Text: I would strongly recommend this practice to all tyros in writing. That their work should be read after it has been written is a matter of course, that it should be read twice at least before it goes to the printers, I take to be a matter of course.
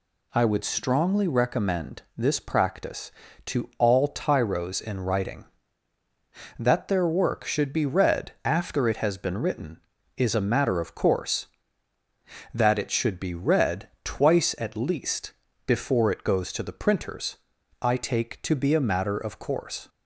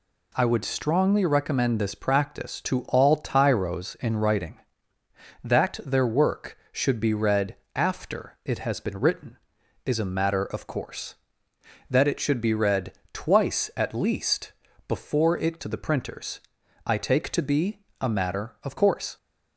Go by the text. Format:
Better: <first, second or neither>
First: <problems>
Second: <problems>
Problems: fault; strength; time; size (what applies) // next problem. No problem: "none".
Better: first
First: pauses between "read" and "twice"; slight; at 13.8 s; 0.16 s long // pauses between "least" and "before"; slight; at 15.3 s; 0.34 s long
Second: pauses between "read" and "after"; slight; at 7.5 s; 0.20 s long // pauses between "read" and "twice"; slight; at 12.9 s; 0.20 s long // pauses between "least" and "before"; slight; at 14.5 s; 0.36 s long // skips "goes"; at 15.5 s // pauses between "be" and "a"; slight; at 17.7 s; 0.22 s long